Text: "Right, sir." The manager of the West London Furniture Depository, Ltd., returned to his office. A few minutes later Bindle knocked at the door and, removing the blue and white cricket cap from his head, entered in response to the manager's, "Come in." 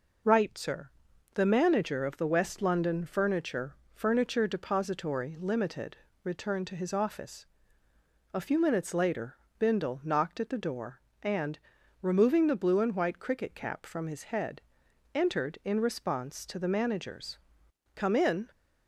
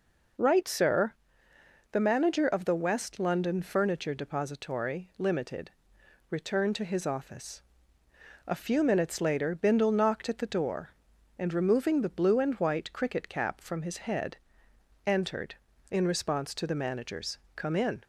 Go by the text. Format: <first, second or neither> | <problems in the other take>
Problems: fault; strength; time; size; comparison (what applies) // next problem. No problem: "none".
second | says "Furniture" twice; at 3.9 s // pauses between "later" and "Bindle"; slight; at 9.3 s; 0.24 s long